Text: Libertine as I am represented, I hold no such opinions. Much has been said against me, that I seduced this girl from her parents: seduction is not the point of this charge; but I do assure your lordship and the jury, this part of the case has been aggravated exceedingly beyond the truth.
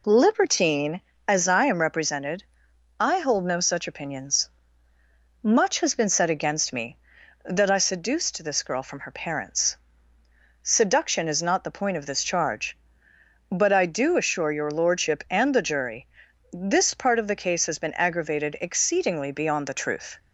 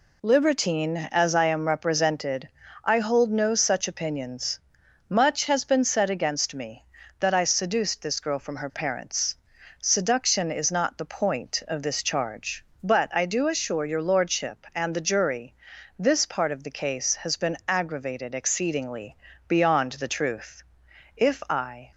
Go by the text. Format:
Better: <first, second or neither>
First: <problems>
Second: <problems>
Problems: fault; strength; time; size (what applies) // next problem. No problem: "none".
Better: first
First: none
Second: pauses between "exceedingly" and "beyond"; slight; at 19.1 s; 0.32 s long // goes on to say "If I"; noticeable; from 21.1 s on; 0.74 s long